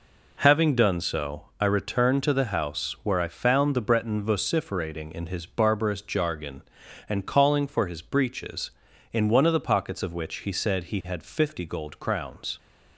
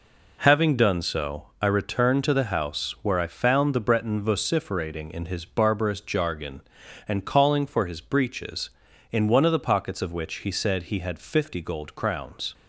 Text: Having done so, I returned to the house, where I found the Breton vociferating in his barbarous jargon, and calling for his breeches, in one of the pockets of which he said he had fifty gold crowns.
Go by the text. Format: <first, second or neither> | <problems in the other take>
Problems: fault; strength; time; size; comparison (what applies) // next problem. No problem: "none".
neither | none